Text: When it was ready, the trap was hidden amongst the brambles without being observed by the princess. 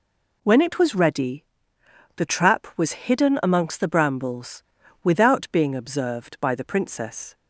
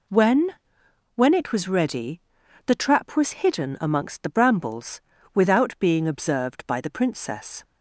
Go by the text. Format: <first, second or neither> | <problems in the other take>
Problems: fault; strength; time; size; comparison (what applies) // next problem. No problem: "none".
first | says "When" twice; at 1.1 s // pauses between "brambles" and "without"; slight; at 5.0 s; 0.32 s long; also in the first